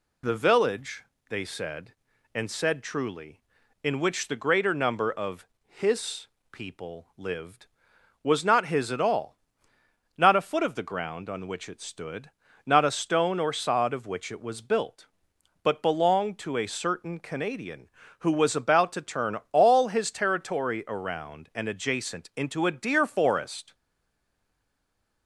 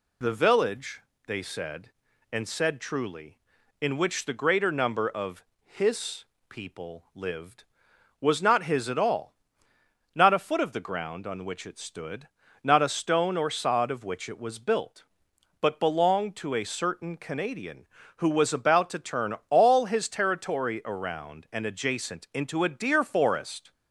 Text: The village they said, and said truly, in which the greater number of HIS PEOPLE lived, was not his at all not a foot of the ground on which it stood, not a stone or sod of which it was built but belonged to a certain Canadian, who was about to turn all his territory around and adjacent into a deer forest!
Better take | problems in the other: second | pauses between "village" and "they"; slight; at 1.0 s; 0.24 s long; slight in the second // pauses between "of" and "HIS"; slight; at 5.4 s; 0.20 s long; slight in the second // pauses between "HIS" and "PEOPLE"; slight; at 6.2 s; 0.22 s long; slight in the second // pauses between "all" and "not"; noticeable; at 9.3 s; 0.80 s long; noticeable in the second // pauses between "turn" and "all"; slight; at 19.3 s; 0.16 s long; slight in the second // stays silent after the last word; noticeable; from 23.7 s on; 1.5 s long

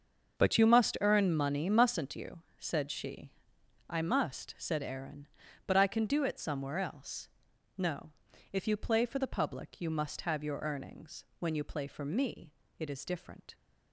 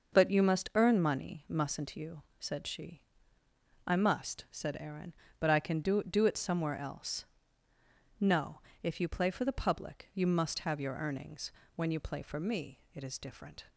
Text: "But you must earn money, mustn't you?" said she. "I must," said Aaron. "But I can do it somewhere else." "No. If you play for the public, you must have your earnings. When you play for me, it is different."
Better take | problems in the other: first | starts louder than the rest; noticeable; until 1.2 s; 6 dB; also in the first // says "do" twice; at 6.0 s

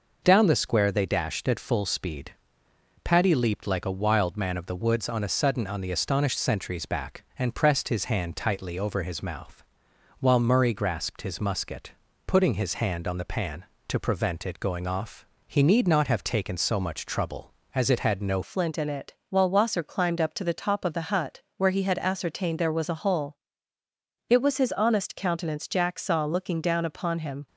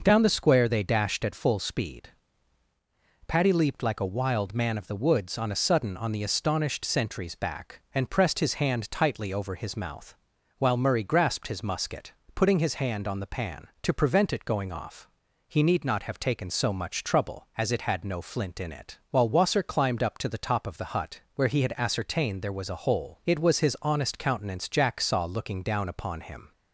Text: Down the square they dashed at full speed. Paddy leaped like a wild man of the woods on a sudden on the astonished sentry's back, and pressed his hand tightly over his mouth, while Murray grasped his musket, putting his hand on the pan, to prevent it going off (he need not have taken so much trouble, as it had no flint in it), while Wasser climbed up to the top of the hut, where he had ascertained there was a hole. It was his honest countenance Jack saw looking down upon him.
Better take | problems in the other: second | changes voice at "flint"; from 18.4 s on; 9.0 s long

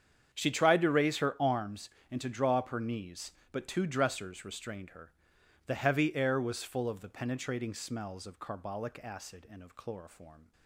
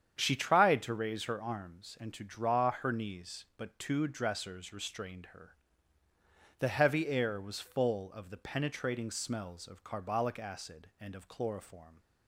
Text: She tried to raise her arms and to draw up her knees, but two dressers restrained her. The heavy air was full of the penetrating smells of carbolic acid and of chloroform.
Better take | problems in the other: first | starts louder than the rest; strong; until 1.2 s; 8.5 dB; strong in the first // skips "up"; at 2.7 s

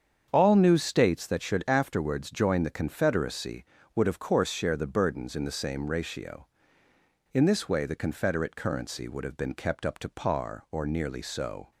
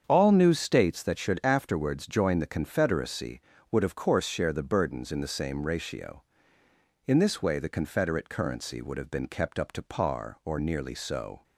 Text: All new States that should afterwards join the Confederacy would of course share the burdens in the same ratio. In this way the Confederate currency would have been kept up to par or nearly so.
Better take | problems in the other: neither | starts louder than the rest; strong; the same in both

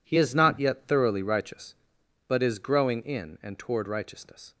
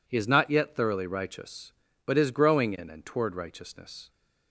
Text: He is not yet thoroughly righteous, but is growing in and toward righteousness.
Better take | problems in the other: neither | none

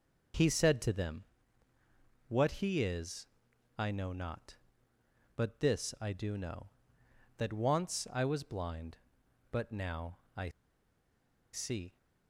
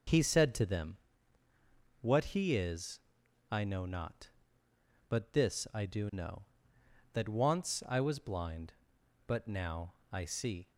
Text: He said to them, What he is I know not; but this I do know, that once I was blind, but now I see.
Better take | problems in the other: second | pauses between "is" and "I"; noticeable; at 3.2 s; 0.54 s long; noticeable in the second // pauses between "now" and "I"; slight; at 10.1 s; 0.18 s long; slight in the second // pauses between "I" and "see"; at 10.4 s; 1.0 s long

